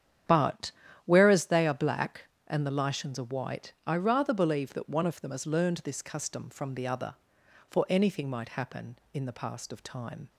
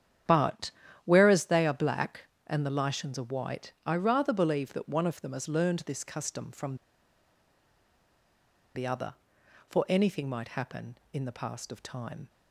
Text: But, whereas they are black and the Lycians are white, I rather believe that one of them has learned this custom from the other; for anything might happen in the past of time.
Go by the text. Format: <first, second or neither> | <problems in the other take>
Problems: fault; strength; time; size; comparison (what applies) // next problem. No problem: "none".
first | starts louder than the rest; strong; until 1.6 s; 9.5 dB; strong in the first // pauses between "from" and "the"; strong; at 6.7 s; 1.9 s long